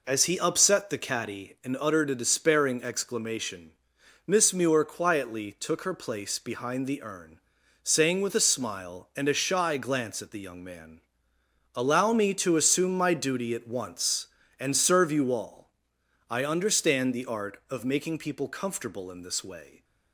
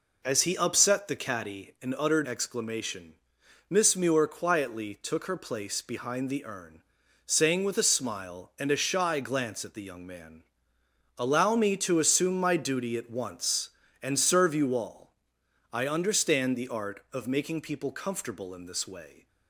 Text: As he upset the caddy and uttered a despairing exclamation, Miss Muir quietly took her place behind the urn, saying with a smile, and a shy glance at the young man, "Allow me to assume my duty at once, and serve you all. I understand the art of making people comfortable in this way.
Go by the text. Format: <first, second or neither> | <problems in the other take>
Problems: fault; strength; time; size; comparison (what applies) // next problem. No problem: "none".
first | skips "a despairing"; at 2.2 s